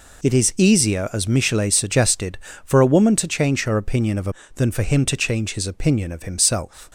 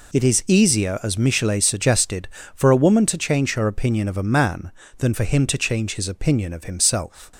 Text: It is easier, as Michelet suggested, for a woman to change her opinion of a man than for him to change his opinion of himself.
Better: second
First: skips "man"; at 4.4 s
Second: none

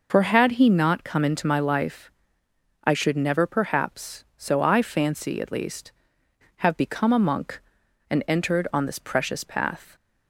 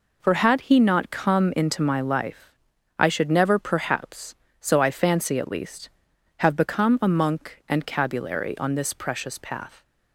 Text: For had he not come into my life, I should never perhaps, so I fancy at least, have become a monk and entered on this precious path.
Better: first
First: none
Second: says "cabulary" for "entered"; at 7.8 s

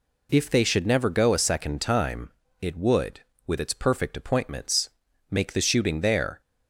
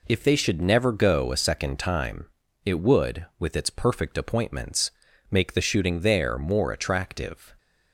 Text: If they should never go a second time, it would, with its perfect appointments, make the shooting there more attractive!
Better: second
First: stops before "more attractive"; at 6.4 s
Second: none

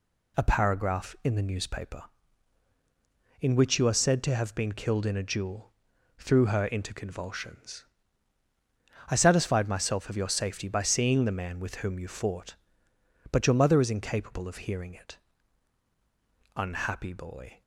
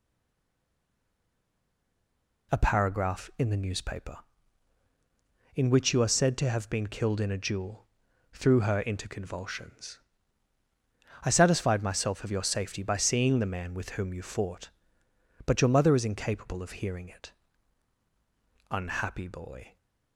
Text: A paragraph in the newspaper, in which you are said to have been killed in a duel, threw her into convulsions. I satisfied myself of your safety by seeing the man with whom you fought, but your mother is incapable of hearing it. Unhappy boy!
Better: first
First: none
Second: stays silent before the first word; until 2.5 s; 2.5 s long

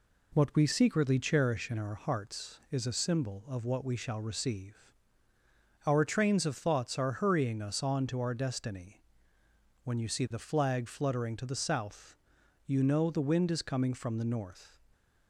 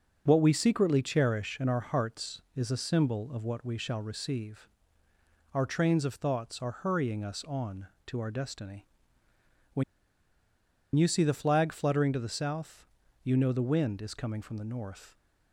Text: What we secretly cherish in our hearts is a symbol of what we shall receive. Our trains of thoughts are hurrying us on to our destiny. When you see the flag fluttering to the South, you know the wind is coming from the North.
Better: first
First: none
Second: starts louder than the rest; noticeable; until 1.2 s; 6 dB // pauses between "When" and "you"; at 9.8 s; 1.1 s long

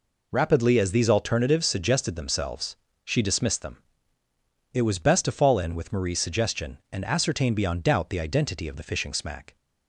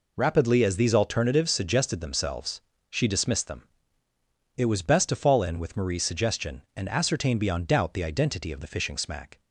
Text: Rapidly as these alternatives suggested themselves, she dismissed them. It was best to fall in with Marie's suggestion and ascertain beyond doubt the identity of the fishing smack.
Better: neither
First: none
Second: none

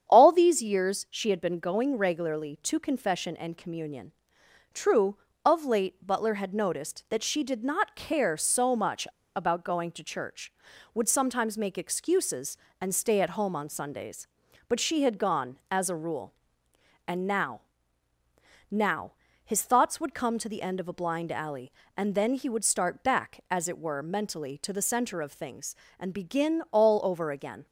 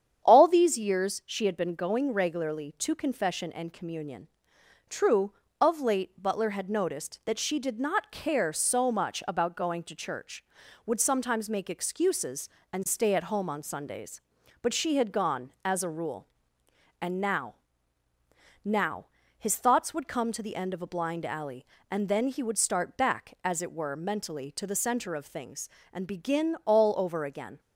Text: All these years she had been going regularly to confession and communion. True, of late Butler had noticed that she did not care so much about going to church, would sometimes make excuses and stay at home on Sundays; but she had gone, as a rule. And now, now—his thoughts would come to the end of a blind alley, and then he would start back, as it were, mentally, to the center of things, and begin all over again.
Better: second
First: starts louder than the rest; strong; until 1.1 s; 8.5 dB // pauses between "much" and "about"; slight; at 9.0 s; 0.30 s long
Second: starts louder than the rest; strong; until 1.3 s; 9 dB

